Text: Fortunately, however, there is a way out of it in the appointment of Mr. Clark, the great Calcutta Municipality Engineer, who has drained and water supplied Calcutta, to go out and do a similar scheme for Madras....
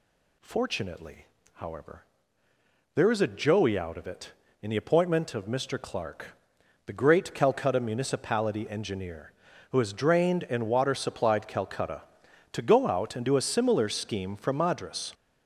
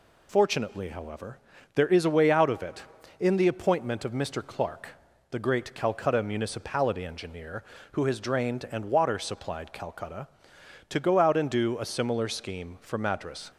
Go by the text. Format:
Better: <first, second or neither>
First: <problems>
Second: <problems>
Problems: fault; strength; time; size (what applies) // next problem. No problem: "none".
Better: second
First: says "joey" for "way"; at 3.2 s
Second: none